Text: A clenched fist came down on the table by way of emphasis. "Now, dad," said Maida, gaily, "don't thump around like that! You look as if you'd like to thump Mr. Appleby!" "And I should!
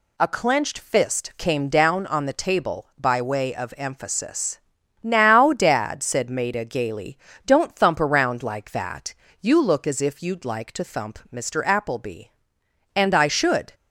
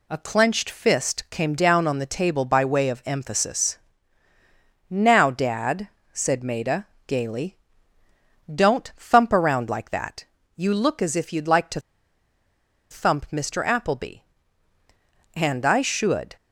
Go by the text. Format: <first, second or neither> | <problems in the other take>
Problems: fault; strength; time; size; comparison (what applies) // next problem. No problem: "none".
first | pauses between "to" and "thump"; at 11.8 s; 1.1 s long